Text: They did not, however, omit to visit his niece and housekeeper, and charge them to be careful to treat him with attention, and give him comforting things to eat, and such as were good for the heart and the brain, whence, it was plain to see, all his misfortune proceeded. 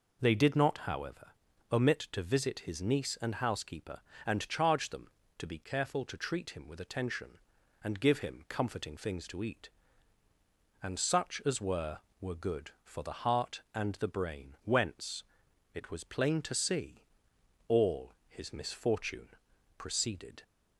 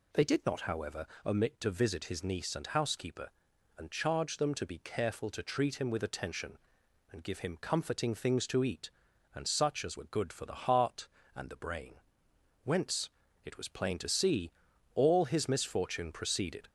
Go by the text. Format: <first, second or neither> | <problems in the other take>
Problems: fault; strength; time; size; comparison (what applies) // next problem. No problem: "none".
second | says "were" twice; at 12.1 s // pauses between "all" and "his"; slight; at 18.1 s; 0.16 s long // pauses between "misfortune" and "proceeded"; noticeable; at 19.2 s; 0.48 s long